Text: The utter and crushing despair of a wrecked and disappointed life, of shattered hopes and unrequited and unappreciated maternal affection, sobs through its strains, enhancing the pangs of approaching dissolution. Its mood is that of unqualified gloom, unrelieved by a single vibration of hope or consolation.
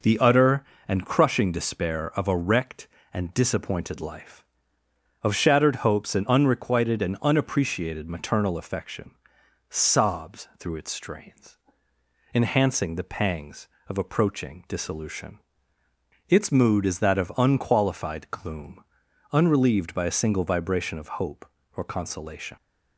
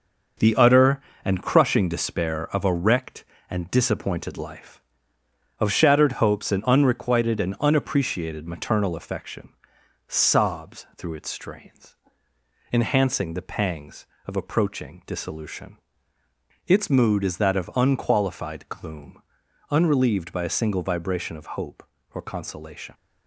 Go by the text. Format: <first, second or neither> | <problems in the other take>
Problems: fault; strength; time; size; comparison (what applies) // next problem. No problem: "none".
first | gets quieter; throughout; 6.5 dB